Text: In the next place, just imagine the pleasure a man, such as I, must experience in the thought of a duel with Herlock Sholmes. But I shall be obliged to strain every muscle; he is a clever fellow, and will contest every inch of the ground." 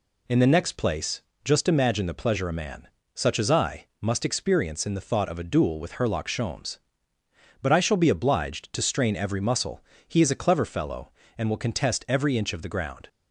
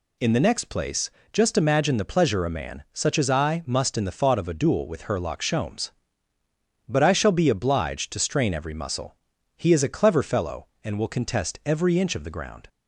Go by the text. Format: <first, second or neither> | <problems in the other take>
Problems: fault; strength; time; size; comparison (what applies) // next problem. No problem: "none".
first | skips "experience"; at 3.9 s